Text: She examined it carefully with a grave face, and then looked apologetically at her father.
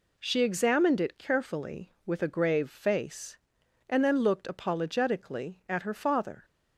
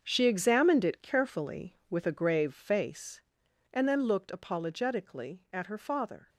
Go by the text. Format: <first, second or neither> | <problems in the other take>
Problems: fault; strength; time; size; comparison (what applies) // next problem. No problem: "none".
first | gets quieter; strong; throughout; 12 dB